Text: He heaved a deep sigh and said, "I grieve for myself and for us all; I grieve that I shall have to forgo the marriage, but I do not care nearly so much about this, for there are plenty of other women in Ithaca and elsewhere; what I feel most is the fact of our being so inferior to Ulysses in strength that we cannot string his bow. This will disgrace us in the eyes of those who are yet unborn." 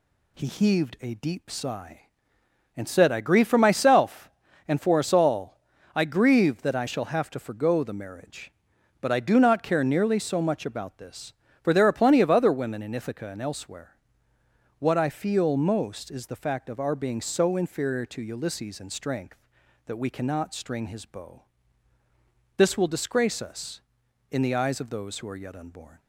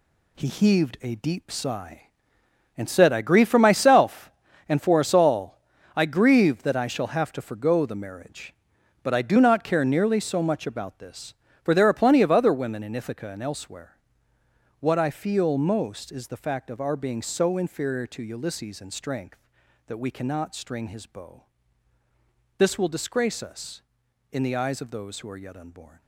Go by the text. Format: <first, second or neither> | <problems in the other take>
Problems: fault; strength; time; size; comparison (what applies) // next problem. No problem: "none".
first | gets quieter; strong; throughout; 9 dB